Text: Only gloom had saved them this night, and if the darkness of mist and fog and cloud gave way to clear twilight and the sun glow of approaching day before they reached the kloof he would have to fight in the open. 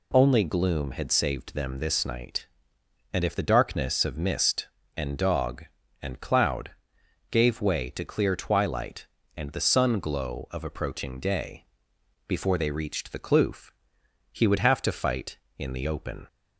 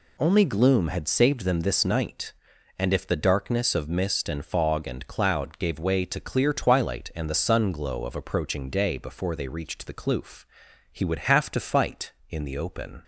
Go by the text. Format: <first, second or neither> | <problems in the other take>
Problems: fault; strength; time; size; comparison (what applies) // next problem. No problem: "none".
second | says "dog" for "fog"; at 5.1 s // pauses between "cloud" and "gave"; noticeable; at 6.7 s; 0.58 s long // pauses between "day" and "before"; noticeable; at 11.6 s; 0.64 s long // pauses between "kloof" and "he"; noticeable; at 13.7 s; 0.60 s long; noticeable in the second